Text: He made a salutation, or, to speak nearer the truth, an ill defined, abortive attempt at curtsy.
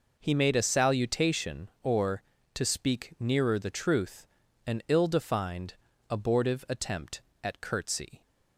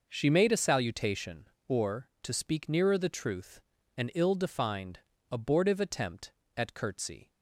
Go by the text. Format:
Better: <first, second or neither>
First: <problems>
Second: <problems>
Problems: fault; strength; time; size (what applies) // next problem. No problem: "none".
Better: first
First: none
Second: says "She" for "He"; at 0.0 s